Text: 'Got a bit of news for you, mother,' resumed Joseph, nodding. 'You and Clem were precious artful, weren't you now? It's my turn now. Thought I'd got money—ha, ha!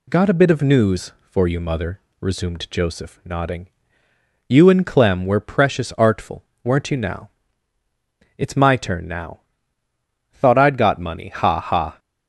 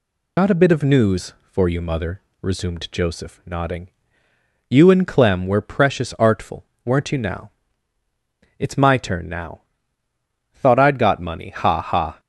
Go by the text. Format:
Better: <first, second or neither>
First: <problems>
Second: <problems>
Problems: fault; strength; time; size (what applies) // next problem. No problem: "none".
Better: first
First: none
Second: loses the start of "Got"; at 0.3 s; 85 ms